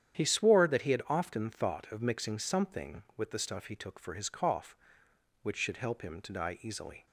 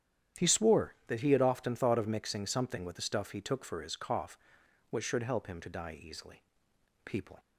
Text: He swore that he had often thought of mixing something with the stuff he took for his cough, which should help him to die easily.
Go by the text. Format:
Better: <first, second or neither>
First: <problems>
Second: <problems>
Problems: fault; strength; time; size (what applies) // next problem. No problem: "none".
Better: first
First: starts louder than the rest; strong; until 1.2 s; 9.5 dB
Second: starts louder than the rest; strong; until 1.5 s; 10 dB // goes on to say "People"; slight; from 7.0 s on; 0.34 s long